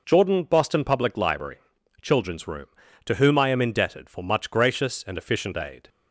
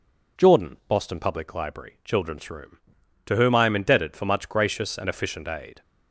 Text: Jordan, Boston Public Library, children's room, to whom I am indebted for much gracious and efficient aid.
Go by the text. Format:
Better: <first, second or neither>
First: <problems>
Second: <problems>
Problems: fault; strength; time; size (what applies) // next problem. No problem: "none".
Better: neither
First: none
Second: none